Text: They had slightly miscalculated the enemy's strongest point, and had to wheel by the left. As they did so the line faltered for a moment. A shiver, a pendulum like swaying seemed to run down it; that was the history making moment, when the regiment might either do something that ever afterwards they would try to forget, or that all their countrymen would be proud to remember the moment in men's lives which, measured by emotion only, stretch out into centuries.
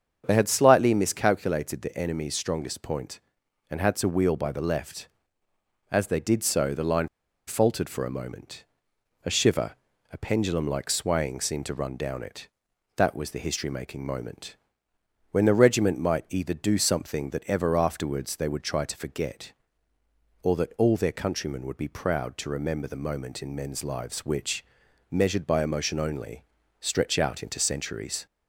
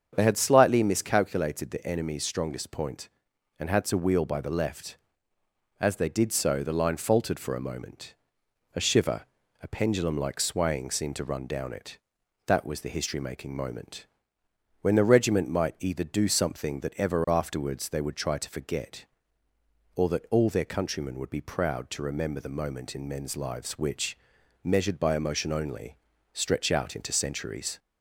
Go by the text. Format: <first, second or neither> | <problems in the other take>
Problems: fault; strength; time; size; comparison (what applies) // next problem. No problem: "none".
second | starts louder than the rest; strong; until 1.2 s; 7.5 dB; strong in the second // pauses between "line" and "faltered"; at 7.0 s; 0.39 s long